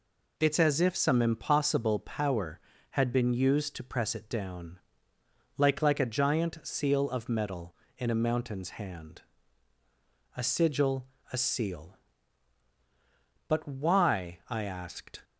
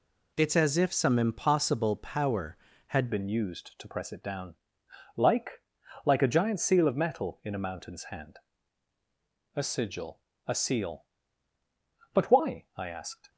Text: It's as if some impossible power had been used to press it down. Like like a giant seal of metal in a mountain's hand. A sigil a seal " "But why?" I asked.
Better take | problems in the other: first | changes voice at "been"; from 3.1 s on; 10.1 s long // pauses between "Like" and "like"; at 5.6 s; 0.42 s long // pauses between "sigil" and "a"; slight; at 10.1 s; 0.28 s long; slight in the first

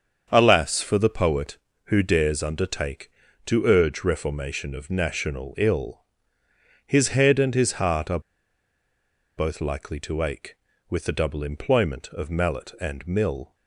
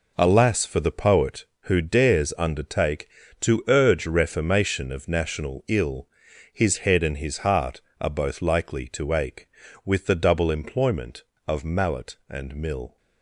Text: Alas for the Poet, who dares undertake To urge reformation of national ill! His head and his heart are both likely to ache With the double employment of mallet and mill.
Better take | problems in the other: second | starts louder than the rest; until 1.3 s; 7 dB // pauses between "are" and "both"; at 8.1 s; 1.1 s long

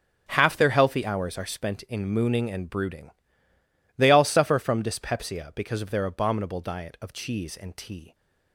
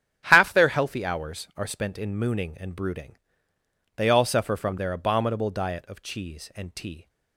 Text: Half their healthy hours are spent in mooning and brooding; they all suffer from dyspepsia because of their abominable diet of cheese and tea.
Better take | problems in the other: first | starts louder than the rest; strong; until 1.2 s; 9 dB; strong in the first // skips "dyspepsia because of"; at 4.7 s

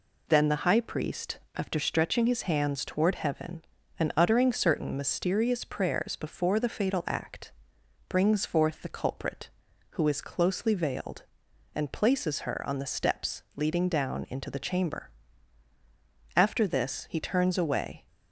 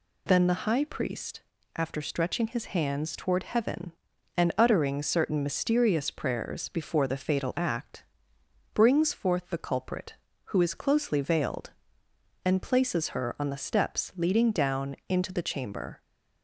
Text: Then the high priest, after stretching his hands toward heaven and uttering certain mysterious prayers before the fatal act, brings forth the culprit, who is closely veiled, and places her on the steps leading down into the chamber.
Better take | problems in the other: second | goes on to say "After this he turns away"; strong; from 16.3 s on; 1.7 s long

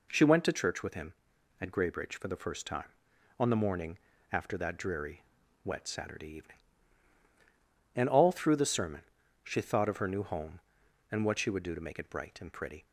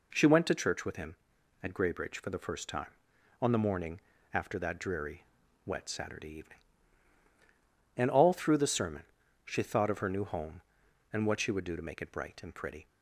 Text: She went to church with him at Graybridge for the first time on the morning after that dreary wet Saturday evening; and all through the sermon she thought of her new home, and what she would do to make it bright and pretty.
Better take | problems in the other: neither | pauses between "morning" and "after"; slight; the same in both // pauses between "dreary" and "wet"; the same in both // pauses between "sermon" and "she"; the same in both

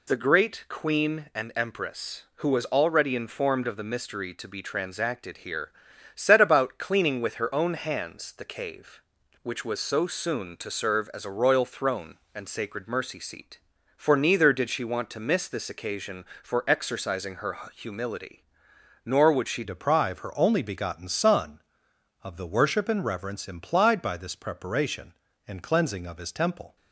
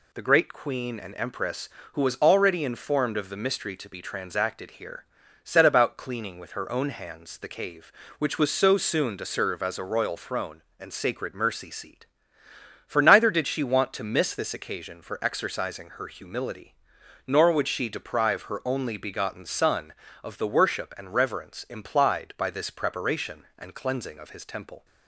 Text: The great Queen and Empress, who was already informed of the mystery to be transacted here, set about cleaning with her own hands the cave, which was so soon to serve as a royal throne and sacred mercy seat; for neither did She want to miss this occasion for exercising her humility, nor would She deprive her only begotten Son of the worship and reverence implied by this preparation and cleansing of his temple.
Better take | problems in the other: second | pauses between "her" and "humility"; slight; at 17.5 s; 0.16 s long // changes voice at "deprive"; from 19.6 s on; 7.1 s long

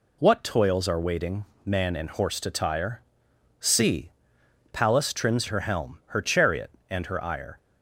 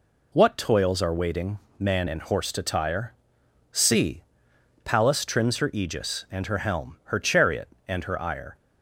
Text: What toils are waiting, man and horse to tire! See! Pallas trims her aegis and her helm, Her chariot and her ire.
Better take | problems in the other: second | skips "her aegis and"; at 5.4 s

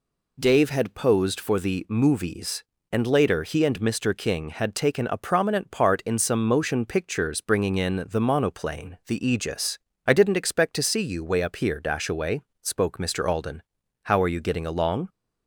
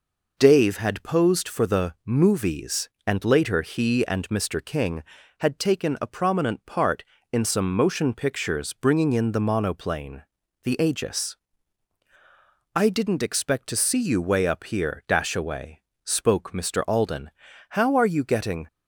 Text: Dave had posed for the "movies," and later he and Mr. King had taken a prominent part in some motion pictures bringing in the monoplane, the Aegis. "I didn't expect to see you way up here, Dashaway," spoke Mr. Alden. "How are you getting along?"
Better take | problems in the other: first | stops before "along"; at 18.6 s

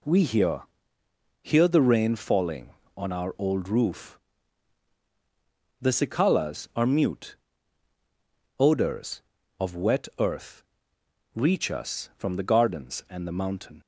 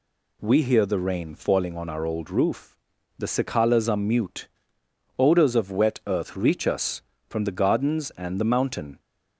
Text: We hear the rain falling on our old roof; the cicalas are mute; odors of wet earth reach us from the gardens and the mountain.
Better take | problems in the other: second | says "hear" twice; at 1.4 s // pauses between "earth" and "reach"; noticeable; at 10.6 s; 0.72 s long

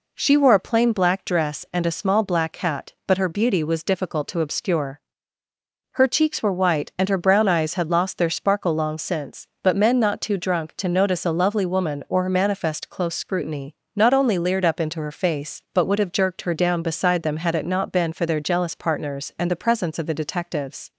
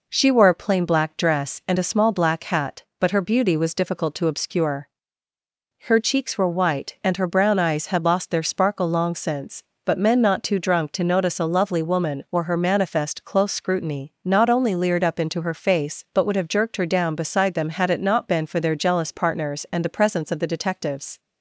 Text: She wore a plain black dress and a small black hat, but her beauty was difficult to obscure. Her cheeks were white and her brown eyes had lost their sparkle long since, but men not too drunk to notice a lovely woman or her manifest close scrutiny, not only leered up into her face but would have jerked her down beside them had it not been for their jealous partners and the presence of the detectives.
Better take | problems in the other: neither | none

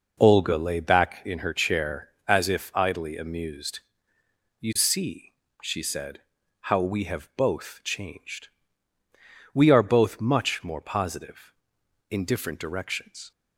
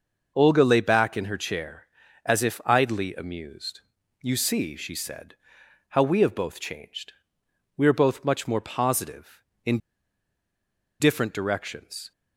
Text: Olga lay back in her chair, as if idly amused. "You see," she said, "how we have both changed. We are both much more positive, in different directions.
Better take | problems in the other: first | pauses between "in" and "different"; at 9.7 s; 1.2 s long

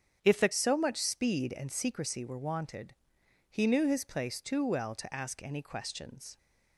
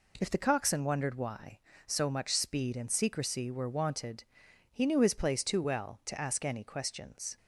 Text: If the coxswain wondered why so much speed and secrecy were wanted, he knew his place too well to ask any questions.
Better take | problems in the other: second | starts louder than the rest; strong; until 1.2 s; 8 dB // skips "coxswain wondered why"; at 0.5 s

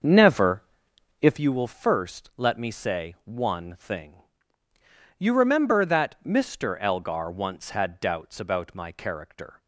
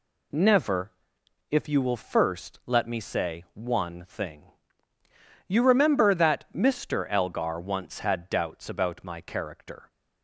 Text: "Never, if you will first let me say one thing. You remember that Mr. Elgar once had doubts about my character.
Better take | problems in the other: second | starts louder than the rest; until 1.5 s; 6.5 dB

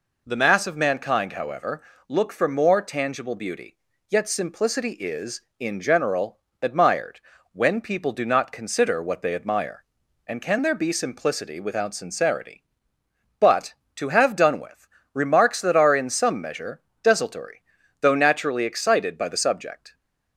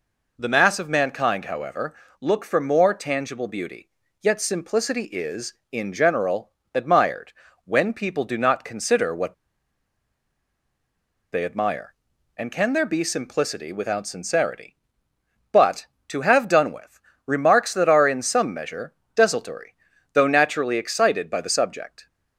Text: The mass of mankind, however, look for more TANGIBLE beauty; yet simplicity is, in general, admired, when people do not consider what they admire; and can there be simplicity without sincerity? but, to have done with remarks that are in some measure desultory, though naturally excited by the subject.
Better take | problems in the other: first | pauses between "what" and "they"; strong; at 9.3 s; 2.0 s long // pauses between "with" and "remarks"; slight; at 16.9 s; 0.24 s long; slight in the first // pauses between "measure" and "desultory"; slight; at 18.9 s; 0.20 s long; slight in the first

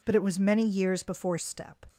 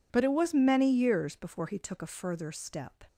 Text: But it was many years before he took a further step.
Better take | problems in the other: second | skips "he took a further"; at 1.3 s

